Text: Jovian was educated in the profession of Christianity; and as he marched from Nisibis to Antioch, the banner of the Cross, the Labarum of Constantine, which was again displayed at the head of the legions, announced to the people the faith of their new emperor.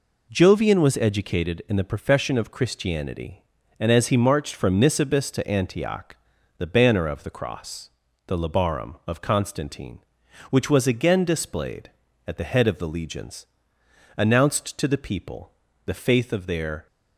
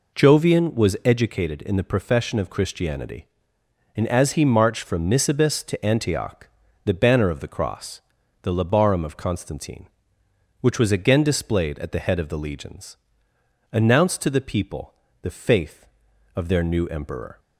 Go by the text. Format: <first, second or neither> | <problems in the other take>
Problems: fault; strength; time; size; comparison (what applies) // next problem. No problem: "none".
second | pauses between "people" and "the"; slight; at 15.5 s; 0.34 s long; slight in the second // stops before "new emperor"; at 16.8 s